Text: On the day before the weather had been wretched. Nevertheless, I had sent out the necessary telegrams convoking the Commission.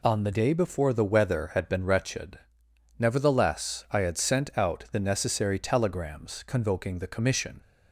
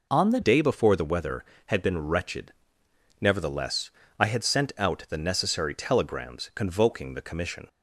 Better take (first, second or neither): first